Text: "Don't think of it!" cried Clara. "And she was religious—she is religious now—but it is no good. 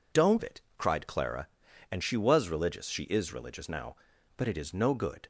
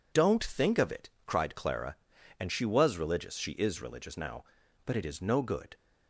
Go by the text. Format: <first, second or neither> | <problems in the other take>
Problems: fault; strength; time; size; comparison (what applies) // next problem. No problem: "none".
second | skips "think of"; at 0.4 s